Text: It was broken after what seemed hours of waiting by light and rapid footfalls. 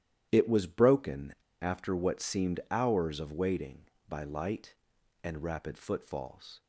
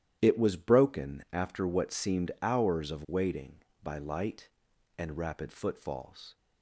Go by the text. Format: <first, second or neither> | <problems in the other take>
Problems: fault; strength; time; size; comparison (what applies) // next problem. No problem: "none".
second | starts louder than the rest; strong; until 1.3 s; 11.5 dB; strong in the second // pauses between "broken" and "after"; slight; at 1.3 s; 0.27 s long